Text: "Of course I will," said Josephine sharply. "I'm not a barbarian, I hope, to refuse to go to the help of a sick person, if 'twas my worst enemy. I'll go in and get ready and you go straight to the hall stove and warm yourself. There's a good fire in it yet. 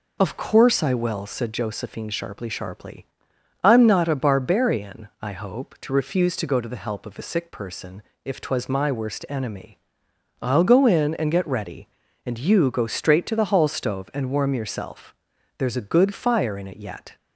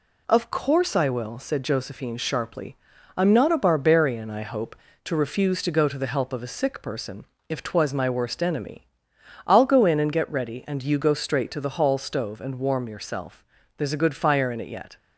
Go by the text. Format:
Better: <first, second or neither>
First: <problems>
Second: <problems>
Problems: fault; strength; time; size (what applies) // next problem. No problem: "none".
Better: second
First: says "sharply" twice; at 2.4 s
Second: none